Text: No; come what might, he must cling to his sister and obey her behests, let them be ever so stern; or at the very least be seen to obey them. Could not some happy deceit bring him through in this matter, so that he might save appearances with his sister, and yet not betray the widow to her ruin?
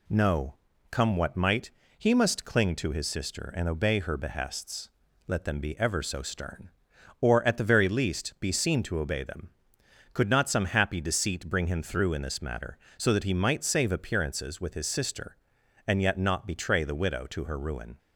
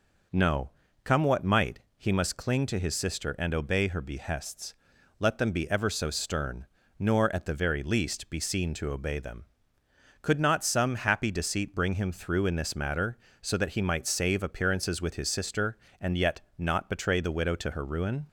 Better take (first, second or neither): first